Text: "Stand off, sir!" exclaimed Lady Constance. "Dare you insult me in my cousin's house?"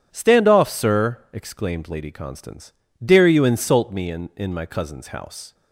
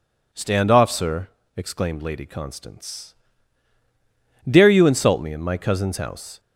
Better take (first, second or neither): second